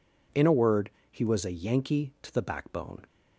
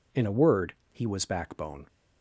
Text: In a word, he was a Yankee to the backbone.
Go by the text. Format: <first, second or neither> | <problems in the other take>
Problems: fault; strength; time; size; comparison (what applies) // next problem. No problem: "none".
first | skips "a Yankee to the"; at 1.2 s